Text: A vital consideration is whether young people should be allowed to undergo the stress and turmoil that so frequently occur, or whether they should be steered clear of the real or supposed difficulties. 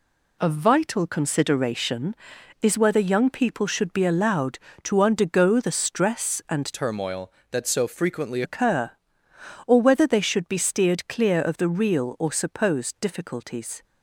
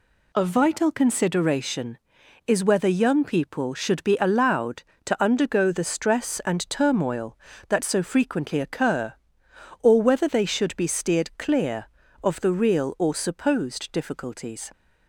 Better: second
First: changes voice from "turmoil" to "frequently"; from 6.7 to 8.4 s; 1.7 s long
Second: none

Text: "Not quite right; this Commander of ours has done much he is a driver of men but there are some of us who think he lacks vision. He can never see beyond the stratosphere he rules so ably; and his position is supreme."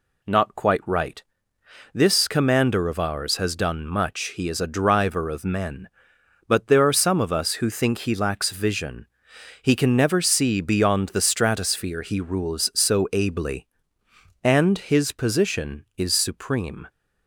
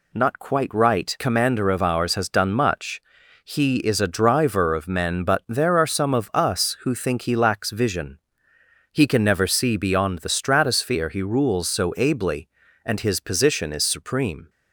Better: first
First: none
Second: skips "this"; at 1.1 s // pauses between "much" and "he"; at 3.0 s; 0.44 s long

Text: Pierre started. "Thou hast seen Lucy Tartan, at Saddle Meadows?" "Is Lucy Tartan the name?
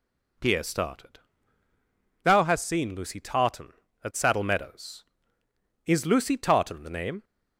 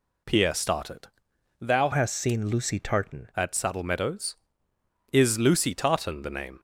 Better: first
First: none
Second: changes voice from "hast" to "Tartan"; from 1.9 to 3.2 s; 1.3 s long

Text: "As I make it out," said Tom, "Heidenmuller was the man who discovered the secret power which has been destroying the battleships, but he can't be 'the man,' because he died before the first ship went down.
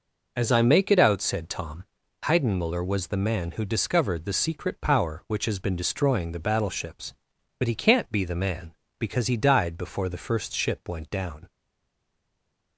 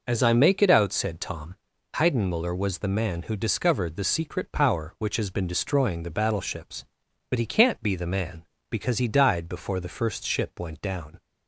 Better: second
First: stays silent after the last word; noticeable; from 11.4 s on; 1.3 s long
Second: none

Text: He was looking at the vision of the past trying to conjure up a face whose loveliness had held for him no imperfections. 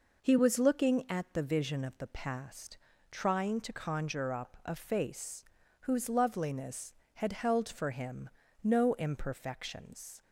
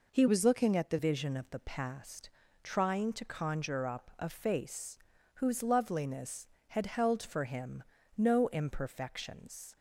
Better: first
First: pauses between "past" and "trying"; slight; at 2.7 s; 0.34 s long // pauses between "face" and "whose"; at 5.4 s; 0.38 s long // pauses between "him" and "no"; slight; at 8.2 s; 0.34 s long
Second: changes voice from "was" to "the"; from 0.2 to 0.9 s; 0.7 s long // pauses between "past" and "trying"; slight; at 2.2 s; 0.34 s long // pauses between "face" and "whose"; at 4.9 s; 0.38 s long // pauses between "him" and "no"; slight; at 7.8 s; 0.34 s long

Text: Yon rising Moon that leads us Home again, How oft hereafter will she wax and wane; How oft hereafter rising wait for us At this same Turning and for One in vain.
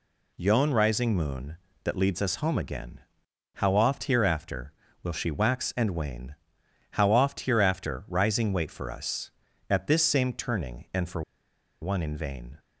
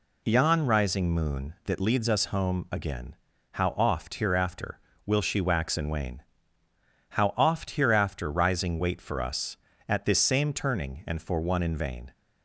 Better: second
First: pauses between "for" and "One"; noticeable; at 11.2 s; 0.60 s long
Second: none

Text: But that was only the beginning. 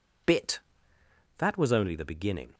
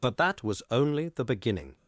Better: second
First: says "Bit" for "But"; at 0.2 s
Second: none

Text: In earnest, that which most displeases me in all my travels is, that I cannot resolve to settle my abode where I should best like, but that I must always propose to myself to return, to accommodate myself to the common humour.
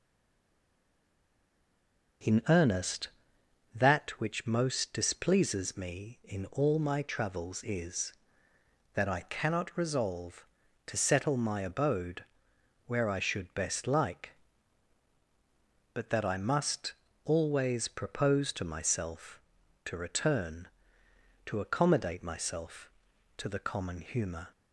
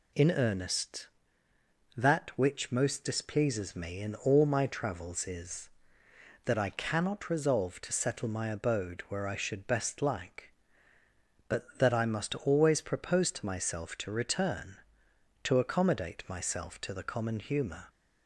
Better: second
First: stays silent before the first word; until 2.2 s; 2.2 s long // starts louder than the rest; until 3.9 s; 6.5 dB // pauses between "abode" and "where"; noticeable; at 12.2 s; 0.62 s long // pauses between "must" and "always"; slight; at 16.9 s; 0.30 s long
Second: none

